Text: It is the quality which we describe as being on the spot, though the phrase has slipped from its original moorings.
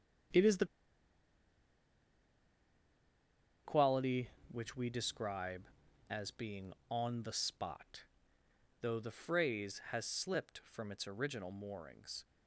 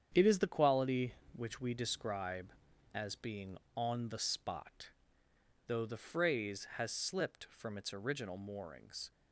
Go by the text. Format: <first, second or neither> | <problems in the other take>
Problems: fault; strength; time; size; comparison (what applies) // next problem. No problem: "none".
second | starts louder than the rest; strong; until 4.5 s; 8.5 dB; strong in the second // pauses between "the" and "quality"; strong; at 0.6 s; 2.9 s long